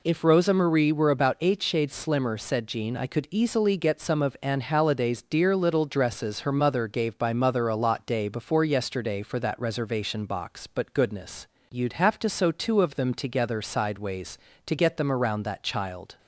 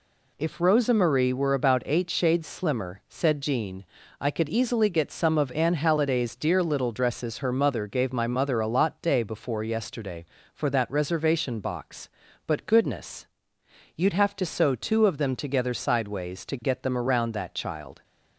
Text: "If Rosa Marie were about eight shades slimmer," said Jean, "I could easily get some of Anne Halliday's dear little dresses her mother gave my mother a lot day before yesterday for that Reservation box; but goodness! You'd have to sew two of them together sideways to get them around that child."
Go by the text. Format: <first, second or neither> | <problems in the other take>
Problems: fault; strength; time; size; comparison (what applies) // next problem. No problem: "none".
second | says "by" for "my"; at 7.1 s